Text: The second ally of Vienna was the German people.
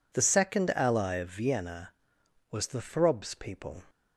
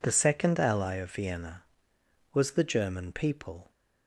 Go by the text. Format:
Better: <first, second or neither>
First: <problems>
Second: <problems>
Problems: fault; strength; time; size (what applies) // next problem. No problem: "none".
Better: second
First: says "Throbs" for "German"; at 2.8 s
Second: none